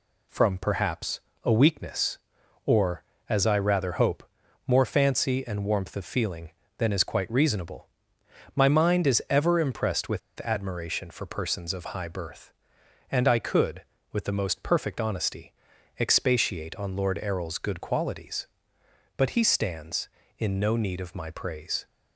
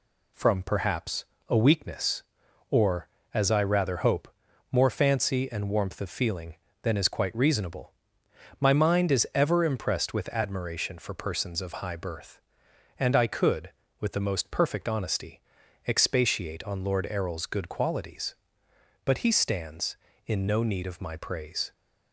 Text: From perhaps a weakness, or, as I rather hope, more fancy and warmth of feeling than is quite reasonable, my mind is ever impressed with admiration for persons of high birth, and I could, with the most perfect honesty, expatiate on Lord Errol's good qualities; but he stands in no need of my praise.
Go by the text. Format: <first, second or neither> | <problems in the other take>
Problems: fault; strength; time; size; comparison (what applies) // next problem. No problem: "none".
second | pauses between "perhaps" and "a"; slight; at 1.1 s; 0.24 s long; slight in the second // pauses between "with" and "admiration"; slight; at 10.1 s; 0.21 s long